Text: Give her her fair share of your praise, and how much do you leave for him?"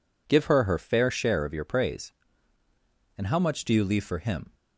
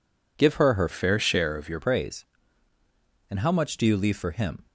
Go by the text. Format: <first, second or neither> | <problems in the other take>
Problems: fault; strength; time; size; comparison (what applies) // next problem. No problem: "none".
first | changes voice from "fair" to "your"; from 0.8 to 1.8 s; 1.0 s long